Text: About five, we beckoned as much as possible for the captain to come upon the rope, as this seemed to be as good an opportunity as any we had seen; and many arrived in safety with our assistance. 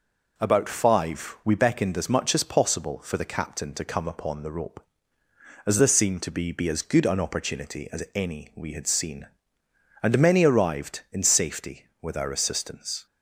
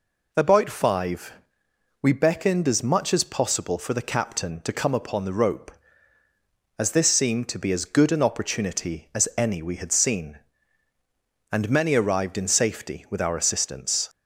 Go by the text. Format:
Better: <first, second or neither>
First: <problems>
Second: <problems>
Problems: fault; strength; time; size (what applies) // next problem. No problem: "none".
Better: second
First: says "be" twice; at 6.5 s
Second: none